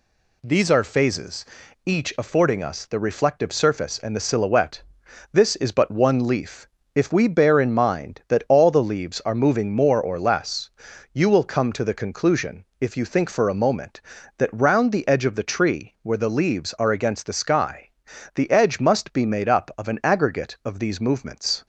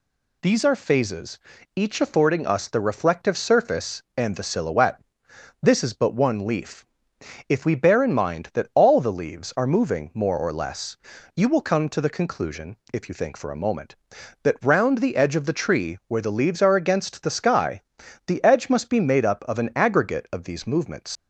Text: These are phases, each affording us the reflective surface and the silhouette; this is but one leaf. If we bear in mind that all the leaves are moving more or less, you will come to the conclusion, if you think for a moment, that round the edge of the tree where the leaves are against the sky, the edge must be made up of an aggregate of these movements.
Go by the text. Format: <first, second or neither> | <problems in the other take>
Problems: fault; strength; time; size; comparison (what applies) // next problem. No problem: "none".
first | leaves "movements" unfinished; at 21.1 s; 105 ms